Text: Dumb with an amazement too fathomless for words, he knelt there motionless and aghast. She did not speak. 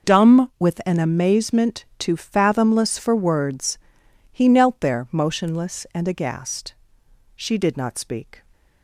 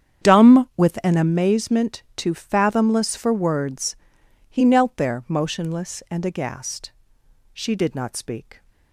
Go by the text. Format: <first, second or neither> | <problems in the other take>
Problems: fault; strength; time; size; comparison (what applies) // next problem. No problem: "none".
first | starts louder than the rest; strong; until 1.4 s; 8.5 dB